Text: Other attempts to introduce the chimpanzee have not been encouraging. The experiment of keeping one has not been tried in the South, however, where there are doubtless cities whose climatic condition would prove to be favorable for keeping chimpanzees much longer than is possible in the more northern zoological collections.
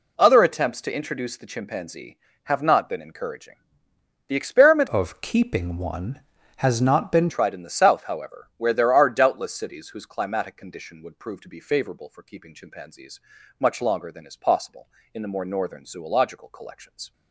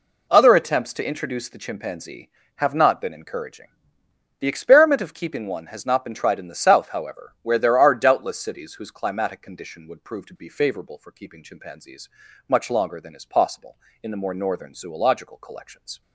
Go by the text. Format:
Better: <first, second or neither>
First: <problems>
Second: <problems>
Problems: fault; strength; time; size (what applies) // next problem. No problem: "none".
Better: second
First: changes voice from "of" to "been"; from 4.8 to 7.2 s; 2.4 s long // pauses between "chimpanzees" and "much"; at 13.1 s; 0.40 s long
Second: pauses between "chimpanzees" and "much"; at 12.0 s; 0.40 s long